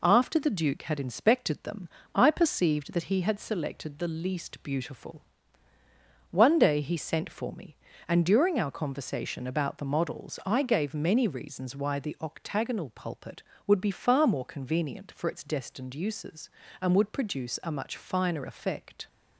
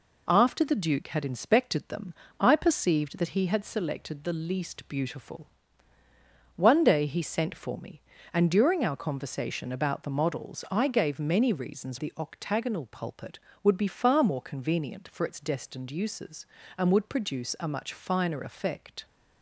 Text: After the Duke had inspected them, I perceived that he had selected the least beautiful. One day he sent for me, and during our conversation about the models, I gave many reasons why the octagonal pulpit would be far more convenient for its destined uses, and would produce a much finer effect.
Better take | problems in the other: first | skips "why"; at 11.9 s

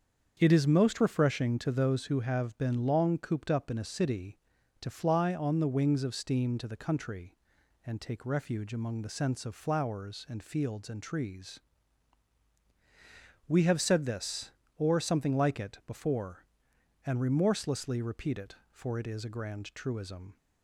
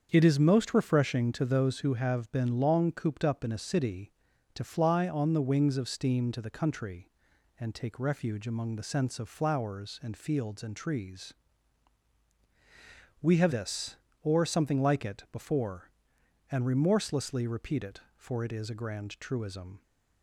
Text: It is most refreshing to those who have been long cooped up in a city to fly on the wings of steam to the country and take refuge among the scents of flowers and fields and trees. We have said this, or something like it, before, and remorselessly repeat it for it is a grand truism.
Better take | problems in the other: first | starts louder than the rest; until 1.1 s; 7 dB; also in the first // skips "said"; at 13.5 s

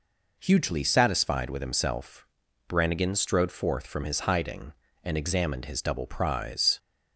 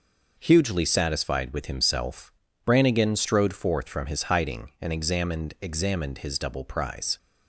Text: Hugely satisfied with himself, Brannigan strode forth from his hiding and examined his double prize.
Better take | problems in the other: first | says "examined" twice; at 5.6 s

